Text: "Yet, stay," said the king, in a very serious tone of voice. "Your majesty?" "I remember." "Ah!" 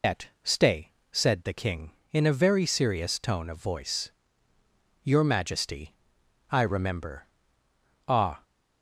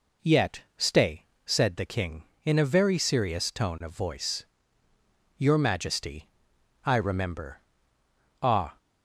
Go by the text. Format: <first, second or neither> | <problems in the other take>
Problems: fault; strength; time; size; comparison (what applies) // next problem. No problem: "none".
second | loses the start of "Yet"; at 0.0 s; 165 ms